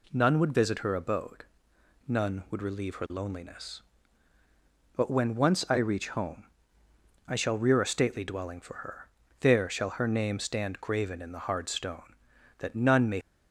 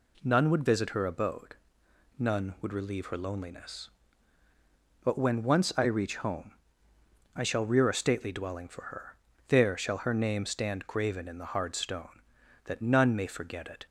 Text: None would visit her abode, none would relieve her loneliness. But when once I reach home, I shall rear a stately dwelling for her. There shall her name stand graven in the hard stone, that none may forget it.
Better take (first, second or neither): second